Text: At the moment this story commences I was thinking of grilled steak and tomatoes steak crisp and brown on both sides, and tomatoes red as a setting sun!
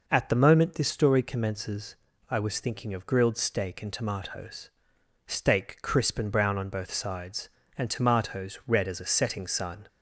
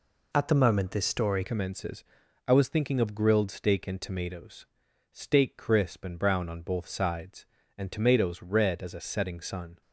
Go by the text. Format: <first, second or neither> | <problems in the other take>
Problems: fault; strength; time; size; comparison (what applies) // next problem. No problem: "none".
first | changes voice at "commences"; from 1.4 s on; 8.4 s long // pauses between "commences" and "I"; at 2.0 s; 0.42 s long; slight in the first // pauses between "tomatoes" and "steak"; noticeable; at 4.6 s; 0.46 s long; noticeable in the first